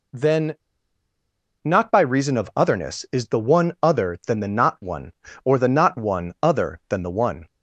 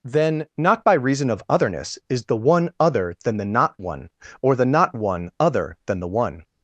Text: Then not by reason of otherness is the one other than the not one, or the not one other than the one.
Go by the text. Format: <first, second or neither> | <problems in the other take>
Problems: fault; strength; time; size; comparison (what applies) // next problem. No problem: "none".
second | pauses between "Then" and "not"; at 0.5 s; 1.0 s long